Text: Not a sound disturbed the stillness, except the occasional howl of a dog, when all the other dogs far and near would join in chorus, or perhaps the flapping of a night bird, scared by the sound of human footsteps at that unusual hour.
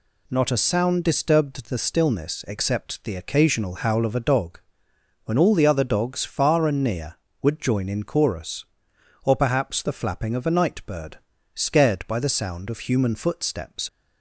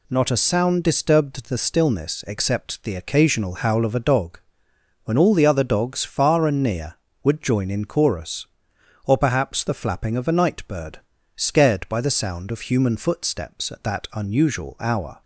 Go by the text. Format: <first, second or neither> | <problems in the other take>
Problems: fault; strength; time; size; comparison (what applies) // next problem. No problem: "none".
second | stops before "at that unusual hour"; at 13.8 s